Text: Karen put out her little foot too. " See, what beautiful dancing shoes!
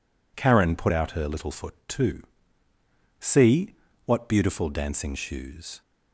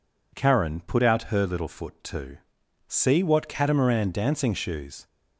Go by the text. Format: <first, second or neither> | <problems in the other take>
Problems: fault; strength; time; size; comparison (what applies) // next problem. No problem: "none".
first | says "catamaran" for "beautiful"; at 3.4 s